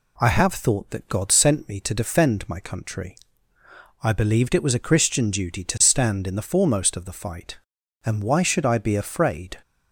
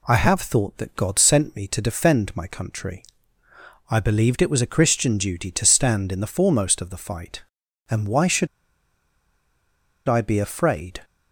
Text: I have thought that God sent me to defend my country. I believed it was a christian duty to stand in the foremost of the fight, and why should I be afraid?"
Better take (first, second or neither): first